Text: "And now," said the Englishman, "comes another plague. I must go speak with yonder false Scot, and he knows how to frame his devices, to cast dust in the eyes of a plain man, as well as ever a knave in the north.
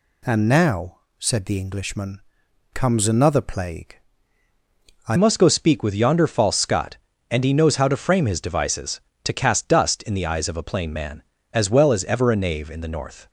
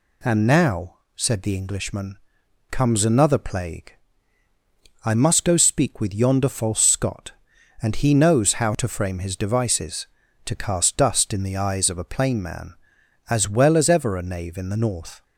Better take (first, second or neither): second